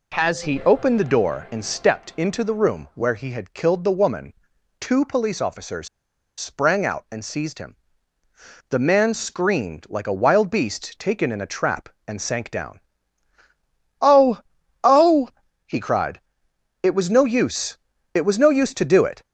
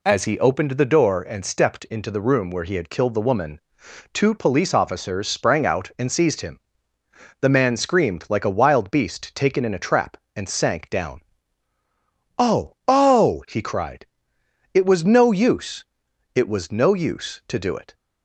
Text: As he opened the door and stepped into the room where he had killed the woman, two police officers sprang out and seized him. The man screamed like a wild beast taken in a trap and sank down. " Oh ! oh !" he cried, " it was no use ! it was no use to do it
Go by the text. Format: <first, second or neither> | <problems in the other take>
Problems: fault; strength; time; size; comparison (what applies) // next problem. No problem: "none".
second | pauses between "officers" and "sprang"; noticeable; at 5.8 s; 0.49 s long